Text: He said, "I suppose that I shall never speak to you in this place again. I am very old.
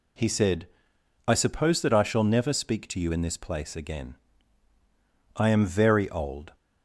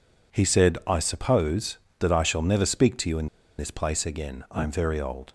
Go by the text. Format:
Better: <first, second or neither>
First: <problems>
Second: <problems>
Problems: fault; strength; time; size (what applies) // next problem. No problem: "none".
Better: first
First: none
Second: pauses between "in" and "this"; slight; at 3.2 s; 0.32 s long